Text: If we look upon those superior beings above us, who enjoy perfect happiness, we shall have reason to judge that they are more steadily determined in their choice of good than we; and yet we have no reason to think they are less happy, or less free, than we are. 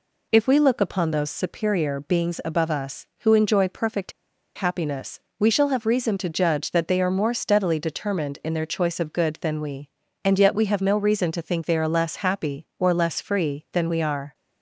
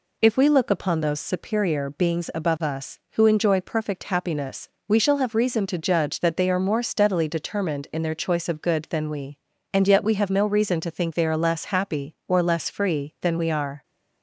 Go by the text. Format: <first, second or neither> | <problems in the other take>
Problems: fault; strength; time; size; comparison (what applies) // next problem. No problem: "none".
second | pauses between "perfect" and "happiness"; at 4.1 s; 0.43 s long